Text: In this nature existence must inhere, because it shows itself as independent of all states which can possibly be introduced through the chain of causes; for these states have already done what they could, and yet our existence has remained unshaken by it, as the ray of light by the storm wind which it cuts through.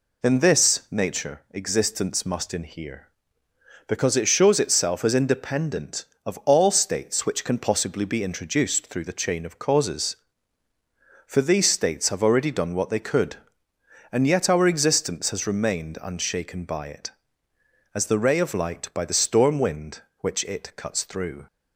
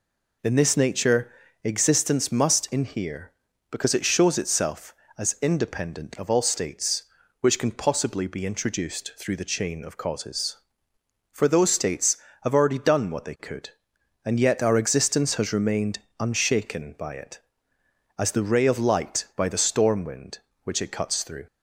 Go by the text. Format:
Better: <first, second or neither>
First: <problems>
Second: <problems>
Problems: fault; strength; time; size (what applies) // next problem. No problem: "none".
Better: first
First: none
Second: pauses between "nature" and "existence"; slight; at 1.3 s; 0.32 s long // says "those" for "these"; at 11.4 s // pauses between "remained" and "unshaken"; slight; at 15.9 s; 0.20 s long